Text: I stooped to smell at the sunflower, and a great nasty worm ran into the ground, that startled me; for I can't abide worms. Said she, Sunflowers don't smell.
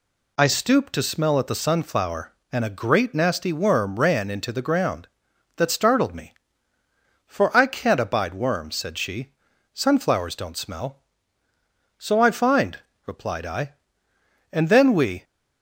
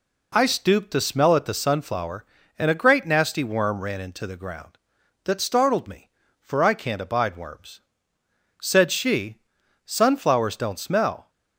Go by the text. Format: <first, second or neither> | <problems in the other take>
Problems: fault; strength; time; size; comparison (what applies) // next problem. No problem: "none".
second | goes on to say "So I find replied I And then we"; strong; from 11.9 s on; 3.2 s long